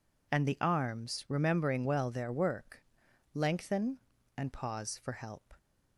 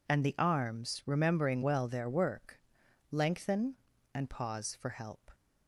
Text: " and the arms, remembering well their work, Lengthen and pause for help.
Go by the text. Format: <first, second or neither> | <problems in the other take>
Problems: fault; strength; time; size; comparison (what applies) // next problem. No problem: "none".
neither | none